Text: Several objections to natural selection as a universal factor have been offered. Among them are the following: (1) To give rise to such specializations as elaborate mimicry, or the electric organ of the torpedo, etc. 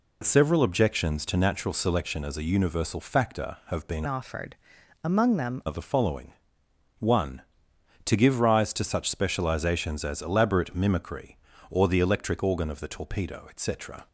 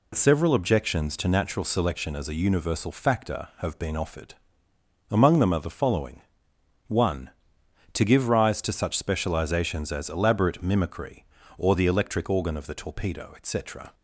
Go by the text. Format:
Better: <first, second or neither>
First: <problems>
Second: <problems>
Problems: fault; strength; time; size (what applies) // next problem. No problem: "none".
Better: second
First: changes voice from "offered" to "them"; from 4.0 to 5.6 s; 1.6 s long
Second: none